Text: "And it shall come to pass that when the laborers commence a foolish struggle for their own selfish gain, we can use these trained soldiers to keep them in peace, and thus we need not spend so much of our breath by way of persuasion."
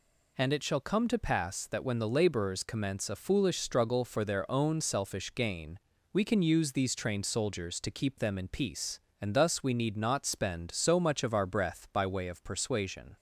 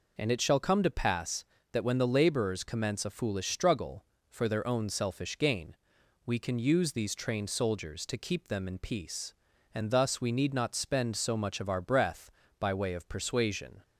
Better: neither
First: none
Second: none

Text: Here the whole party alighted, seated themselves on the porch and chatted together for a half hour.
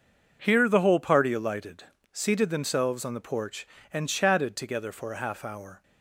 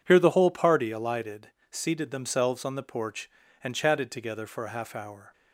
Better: neither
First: none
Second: none

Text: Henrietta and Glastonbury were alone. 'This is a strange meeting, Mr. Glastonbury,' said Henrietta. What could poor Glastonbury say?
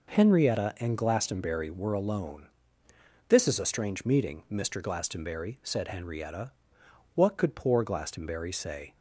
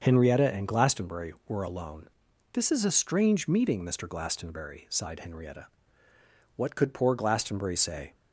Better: first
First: none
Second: starts louder than the rest; until 1.0 s; 6.5 dB // says "sighed" for "said"; at 4.8 s

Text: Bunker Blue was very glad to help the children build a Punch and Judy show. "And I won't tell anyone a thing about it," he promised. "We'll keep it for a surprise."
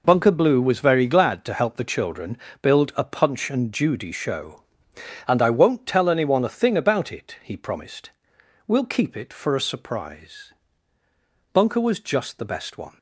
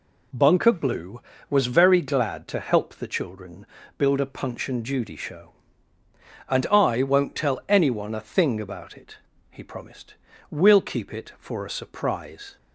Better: second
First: pauses between "children" and "build"; slight; at 2.3 s; 0.24 s long // goes on to say "Bunker was just the best one"; from 11.5 s on; 1.4 s long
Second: pauses between "children" and "build"; slight; at 3.6 s; 0.32 s long

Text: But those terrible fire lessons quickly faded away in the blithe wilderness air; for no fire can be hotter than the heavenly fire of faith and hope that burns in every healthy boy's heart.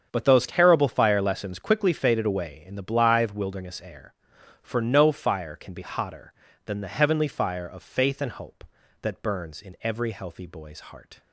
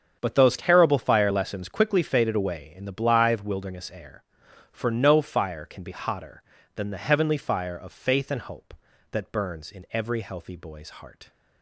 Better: neither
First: starts louder than the rest; strong; until 1.1 s; 7.5 dB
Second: starts louder than the rest; strong; until 1.2 s; 7.5 dB

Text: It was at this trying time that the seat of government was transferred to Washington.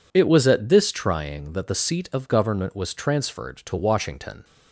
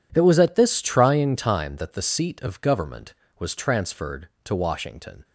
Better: second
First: skips "time"; at 1.5 s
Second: none

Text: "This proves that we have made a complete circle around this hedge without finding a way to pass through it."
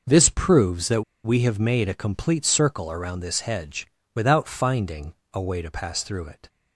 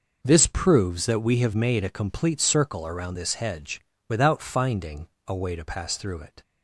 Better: second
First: pauses between "that" and "we"; slight; at 1.0 s; 0.22 s long // pauses between "hedge" and "without"; slight; at 3.8 s; 0.28 s long // pauses between "finding" and "a"; slight; at 5.1 s; 0.22 s long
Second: pauses between "hedge" and "without"; slight; at 3.8 s; 0.28 s long // pauses between "finding" and "a"; slight; at 5.0 s; 0.22 s long

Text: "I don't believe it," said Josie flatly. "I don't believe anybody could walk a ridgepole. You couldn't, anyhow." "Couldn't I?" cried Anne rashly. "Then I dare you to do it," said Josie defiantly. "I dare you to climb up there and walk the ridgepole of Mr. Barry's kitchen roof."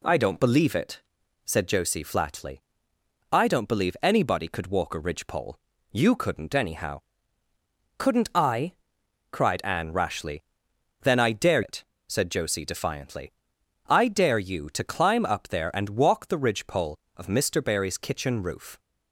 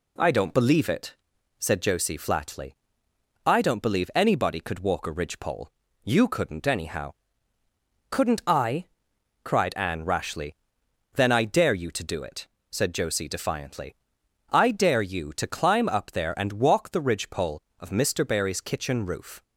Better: second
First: skips "you to do"; at 11.6 s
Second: none

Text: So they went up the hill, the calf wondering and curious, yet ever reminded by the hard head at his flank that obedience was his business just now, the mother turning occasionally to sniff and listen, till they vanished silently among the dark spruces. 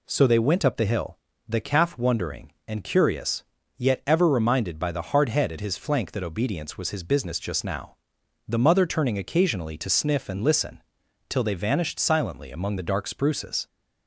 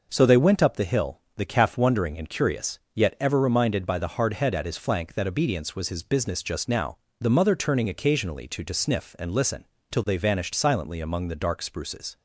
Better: first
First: none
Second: says "to" twice; at 8.6 s

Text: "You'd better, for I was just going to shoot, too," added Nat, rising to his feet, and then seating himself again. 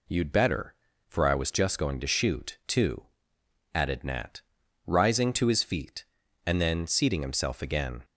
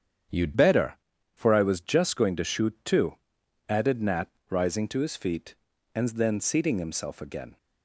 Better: first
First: none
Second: starts louder than the rest; strong; until 1.7 s; 8.5 dB // changes voice at "better"; from 0.5 s on; 7.0 s long

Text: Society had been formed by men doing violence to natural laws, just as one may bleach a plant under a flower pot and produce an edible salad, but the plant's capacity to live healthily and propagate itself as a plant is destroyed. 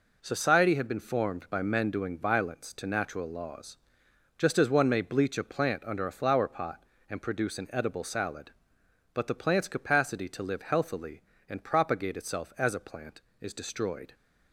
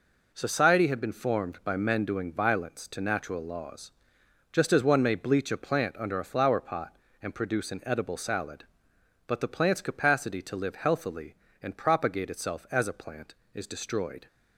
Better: neither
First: none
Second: none

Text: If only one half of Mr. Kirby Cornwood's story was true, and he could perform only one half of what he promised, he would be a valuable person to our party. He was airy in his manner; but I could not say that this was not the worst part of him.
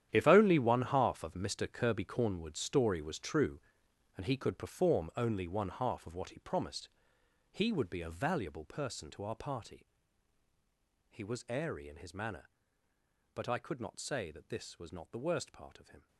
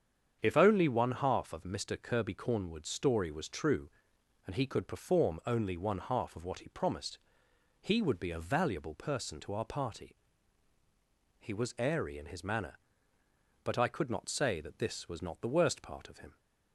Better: second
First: gets quieter; strong; throughout; 14.5 dB // starts louder than the rest; strong; until 1.1 s; 10.5 dB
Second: starts louder than the rest; strong; until 1.4 s; 8 dB

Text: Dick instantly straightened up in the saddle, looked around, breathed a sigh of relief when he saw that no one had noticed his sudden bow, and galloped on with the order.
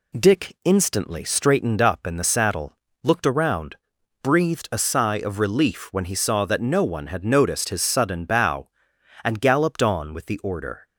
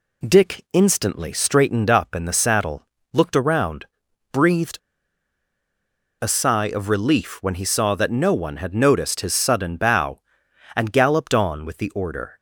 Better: first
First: none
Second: pauses between "breathed" and "a"; strong; at 4.7 s; 1.4 s long

